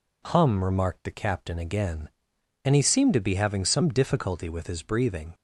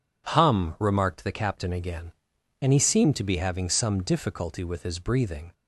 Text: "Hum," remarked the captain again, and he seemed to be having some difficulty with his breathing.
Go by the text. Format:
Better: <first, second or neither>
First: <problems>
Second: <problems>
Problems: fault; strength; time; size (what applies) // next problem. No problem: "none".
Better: neither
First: none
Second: none